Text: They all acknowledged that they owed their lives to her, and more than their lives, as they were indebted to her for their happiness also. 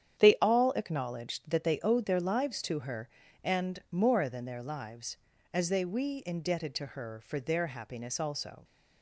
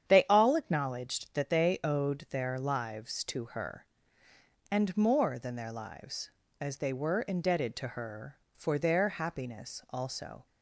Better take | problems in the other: second | starts louder than the rest; strong; until 1.2 s; 9 dB; strong in the second // says "we" for "were"; at 5.8 s

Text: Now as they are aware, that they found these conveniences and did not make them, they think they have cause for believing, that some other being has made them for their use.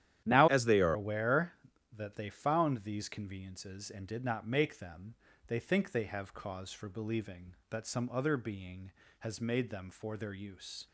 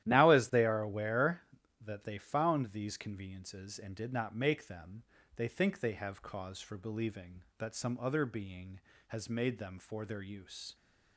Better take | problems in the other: second | starts louder than the rest; strong; until 1.2 s; 11.5 dB; strong in the second // changes voice from "as" to "are"; from 0.4 to 0.9 s; 0.5 s long

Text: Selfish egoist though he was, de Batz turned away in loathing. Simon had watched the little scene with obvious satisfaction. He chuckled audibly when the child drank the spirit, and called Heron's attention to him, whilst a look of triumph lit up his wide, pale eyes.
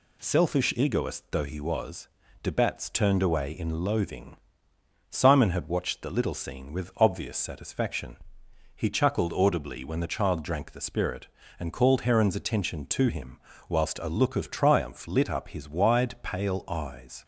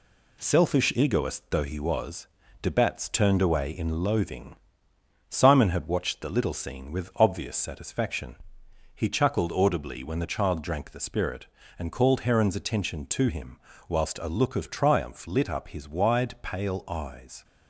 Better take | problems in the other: first | gets quieter; noticeable; throughout; 4.5 dB

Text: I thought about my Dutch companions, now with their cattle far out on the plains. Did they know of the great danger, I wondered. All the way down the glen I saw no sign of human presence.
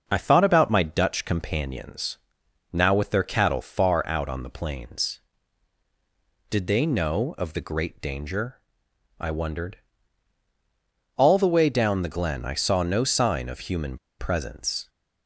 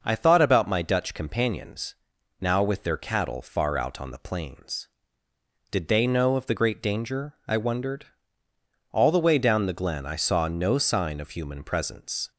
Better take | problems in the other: second | pauses between "human" and "presence"; slight; at 13.9 s; 0.22 s long

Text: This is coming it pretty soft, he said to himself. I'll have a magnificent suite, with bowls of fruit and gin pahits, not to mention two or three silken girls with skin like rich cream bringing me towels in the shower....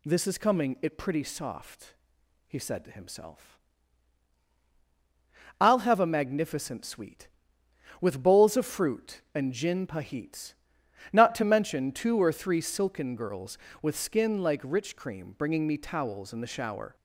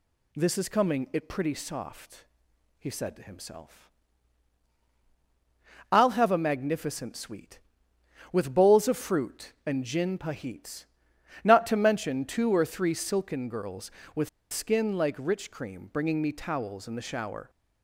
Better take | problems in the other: first | pauses between "with" and "skin"; slight; at 14.2 s; 0.24 s long

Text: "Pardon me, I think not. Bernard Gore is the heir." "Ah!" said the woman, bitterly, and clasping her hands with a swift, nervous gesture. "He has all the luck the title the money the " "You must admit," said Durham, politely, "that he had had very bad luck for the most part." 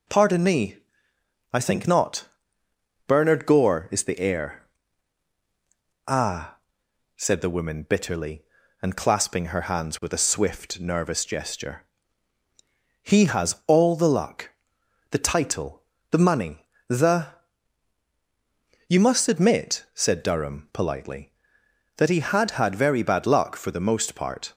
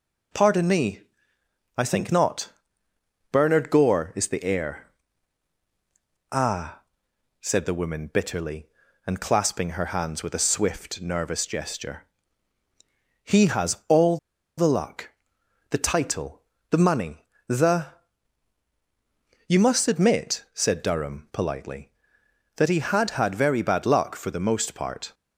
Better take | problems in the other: first | pauses between "all" and "the"; at 14.1 s; 0.40 s long // pauses between "luck" and "the"; noticeable; at 15.0 s; 0.60 s long; noticeable in the first // pauses between "title" and "the"; slight; at 16.4 s; 0.28 s long; slight in the first // pauses between "money" and "the"; slight; at 17.2 s; 0.22 s long; slight in the first

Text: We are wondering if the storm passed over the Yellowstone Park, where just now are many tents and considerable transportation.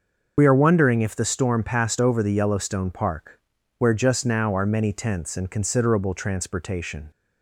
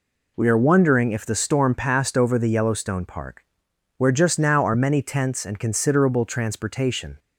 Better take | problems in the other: second | loses the start of "We"; at 0.3 s; 65 ms // starts louder than the rest; noticeable; until 1.3 s; 6 dB

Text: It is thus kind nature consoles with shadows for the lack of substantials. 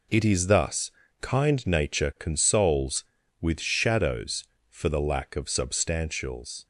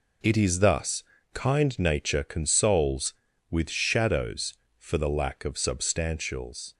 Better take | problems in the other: neither | pauses between "thus" and "kind"; slight; the same in both

